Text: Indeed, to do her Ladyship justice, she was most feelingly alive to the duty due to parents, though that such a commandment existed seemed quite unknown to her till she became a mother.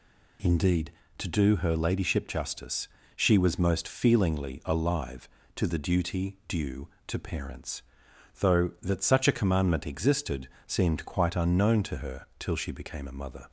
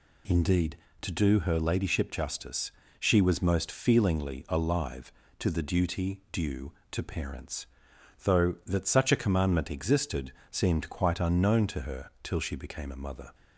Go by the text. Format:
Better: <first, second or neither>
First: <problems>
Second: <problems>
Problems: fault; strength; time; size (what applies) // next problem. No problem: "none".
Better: neither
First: pauses between "existed" and "seemed"; slight; at 10.4 s; 0.18 s long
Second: pauses between "existed" and "seemed"; slight; at 10.3 s; 0.18 s long